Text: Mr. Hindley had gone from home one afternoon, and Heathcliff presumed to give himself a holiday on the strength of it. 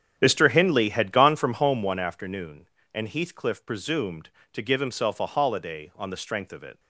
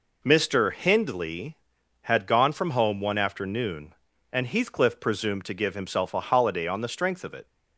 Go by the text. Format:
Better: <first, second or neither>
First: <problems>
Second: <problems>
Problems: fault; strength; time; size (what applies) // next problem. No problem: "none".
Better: second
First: starts louder than the rest; strong; until 2.0 s; 8.5 dB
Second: none